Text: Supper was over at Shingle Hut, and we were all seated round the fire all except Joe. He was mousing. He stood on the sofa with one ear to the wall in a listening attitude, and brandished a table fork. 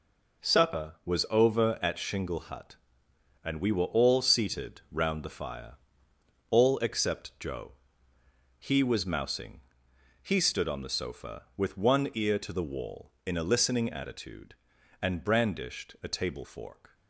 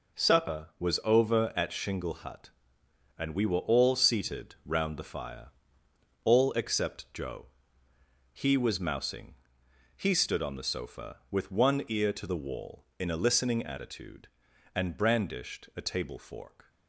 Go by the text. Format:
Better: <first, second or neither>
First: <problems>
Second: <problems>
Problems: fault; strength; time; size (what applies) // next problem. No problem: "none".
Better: neither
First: pauses between "fire" and "all"; noticeable; at 5.7 s; 0.78 s long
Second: pauses between "fire" and "all"; noticeable; at 5.4 s; 0.78 s long